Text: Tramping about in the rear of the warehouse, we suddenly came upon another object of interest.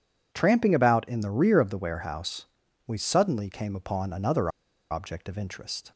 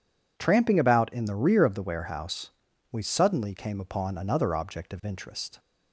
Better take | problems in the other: second | pauses between "another" and "object"; at 4.4 s; 0.41 s long

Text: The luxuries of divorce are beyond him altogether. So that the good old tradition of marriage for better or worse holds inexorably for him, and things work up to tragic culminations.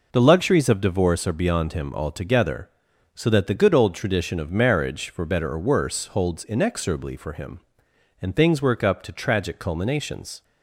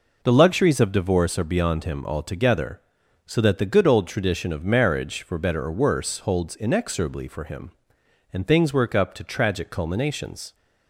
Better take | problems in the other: neither | none

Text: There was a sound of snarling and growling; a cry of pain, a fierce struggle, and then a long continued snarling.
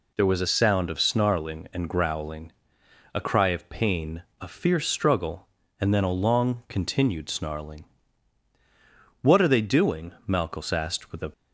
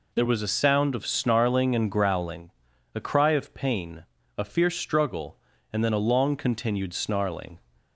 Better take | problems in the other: second | goes on to say "What are they doing Malchus asked with a"; strong; from 9.2 s on; 2.0 s long

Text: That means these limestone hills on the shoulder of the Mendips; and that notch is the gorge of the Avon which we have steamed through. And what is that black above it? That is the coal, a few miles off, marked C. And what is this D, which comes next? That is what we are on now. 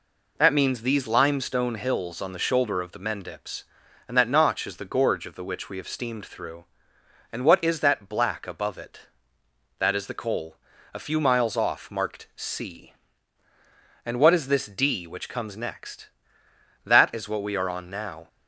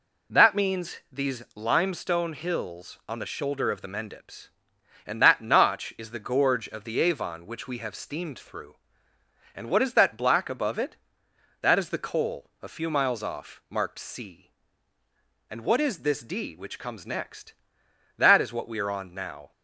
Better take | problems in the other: second | skips "Avon"; at 5.4 s

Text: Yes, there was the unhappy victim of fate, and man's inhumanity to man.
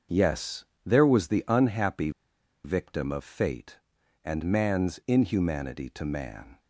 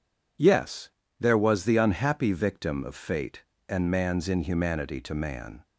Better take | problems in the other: second | starts louder than the rest; until 1.3 s; 6.5 dB // pauses between "unhappy" and "victim"; noticeable; at 2.0 s; 0.54 s long

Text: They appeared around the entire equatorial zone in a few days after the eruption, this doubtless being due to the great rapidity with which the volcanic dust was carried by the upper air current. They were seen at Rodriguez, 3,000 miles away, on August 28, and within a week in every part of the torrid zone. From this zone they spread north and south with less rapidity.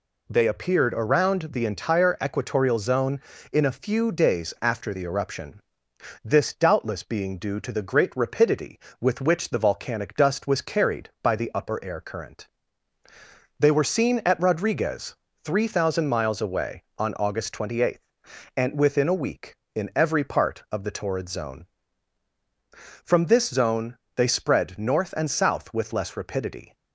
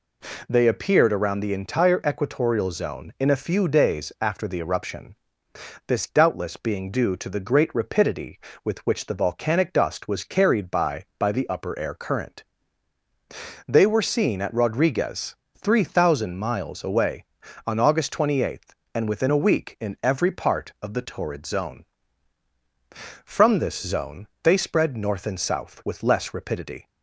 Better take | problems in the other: first | says "by" twice; at 11.1 s // pauses between "zone" and "they"; slight; at 24.2 s; 0.16 s long; slight in the first

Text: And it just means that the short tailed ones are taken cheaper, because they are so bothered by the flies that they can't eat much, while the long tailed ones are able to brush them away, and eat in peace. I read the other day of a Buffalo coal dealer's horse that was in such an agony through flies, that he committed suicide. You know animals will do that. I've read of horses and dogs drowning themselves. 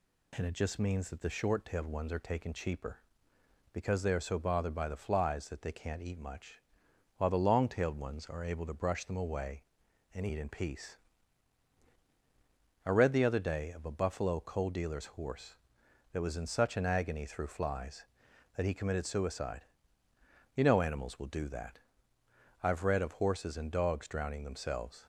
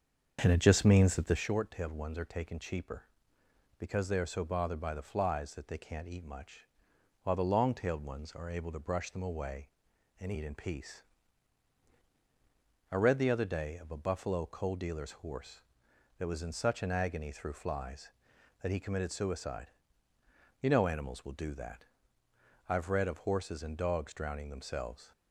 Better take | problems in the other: first | starts louder than the rest; until 1.5 s; 6.5 dB

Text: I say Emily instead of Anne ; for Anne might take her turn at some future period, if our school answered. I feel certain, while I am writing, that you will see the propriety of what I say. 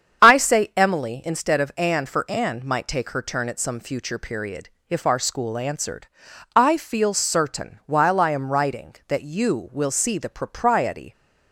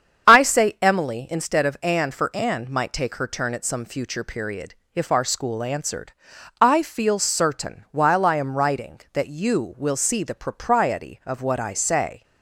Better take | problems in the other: second | starts louder than the rest; strong; until 1.3 s; 8 dB; strong in the second // stops before "of what I say"; at 11.1 s

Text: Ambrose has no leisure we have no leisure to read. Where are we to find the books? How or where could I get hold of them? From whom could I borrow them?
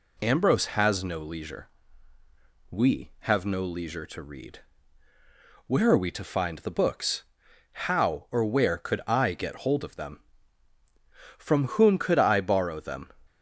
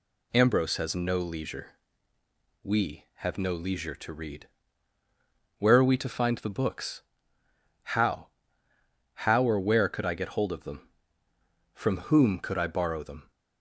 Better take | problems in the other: first | pauses between "leisure" and "we"; noticeable; at 1.6 s; 0.92 s long; also in the first // says "How" twice; at 9.2 s

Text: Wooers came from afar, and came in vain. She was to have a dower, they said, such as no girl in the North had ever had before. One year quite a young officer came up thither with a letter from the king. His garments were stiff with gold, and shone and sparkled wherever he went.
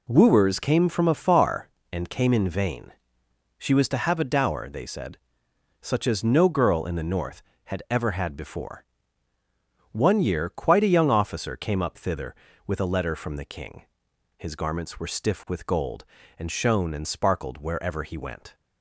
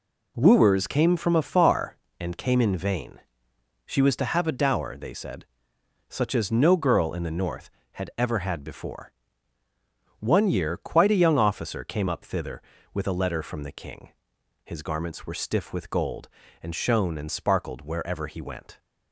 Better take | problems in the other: neither | none

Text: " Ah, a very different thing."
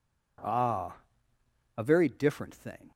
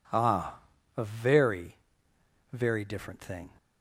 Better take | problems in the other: first | says "very" twice; at 2.5 s

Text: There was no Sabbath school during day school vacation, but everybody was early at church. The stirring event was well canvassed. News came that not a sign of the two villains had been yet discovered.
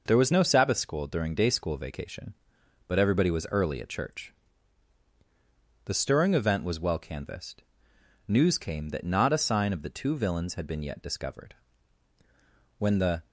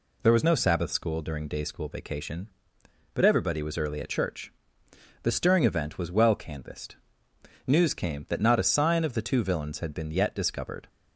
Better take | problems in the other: second | goes on to say "When the"; slight; from 12.7 s on; 0.48 s long

